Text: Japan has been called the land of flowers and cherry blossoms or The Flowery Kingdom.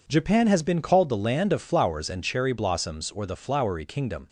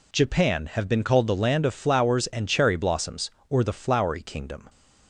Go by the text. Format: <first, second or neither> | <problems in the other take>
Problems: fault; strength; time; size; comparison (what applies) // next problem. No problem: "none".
first | says "have" for "has"; at 0.7 s